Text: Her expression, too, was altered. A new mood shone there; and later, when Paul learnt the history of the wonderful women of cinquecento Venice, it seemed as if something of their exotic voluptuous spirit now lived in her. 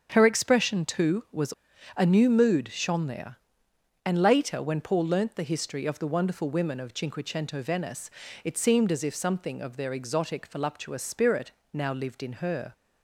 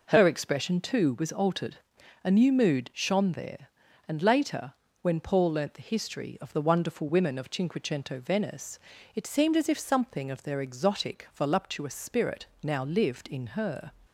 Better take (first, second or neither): second